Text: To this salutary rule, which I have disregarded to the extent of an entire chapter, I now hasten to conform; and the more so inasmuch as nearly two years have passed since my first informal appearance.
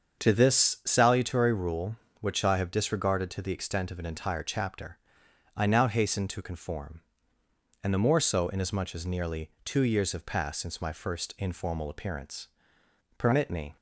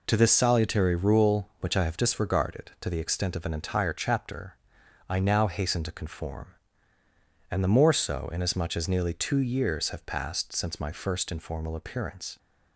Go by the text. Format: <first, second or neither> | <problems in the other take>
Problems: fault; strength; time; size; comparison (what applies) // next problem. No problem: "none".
second | starts louder than the rest; until 1.2 s; 7 dB // pauses between "nearly" and "two"; slight; at 9.4 s; 0.16 s long // goes on to say "Permit me"; from 13.1 s on; 0.60 s long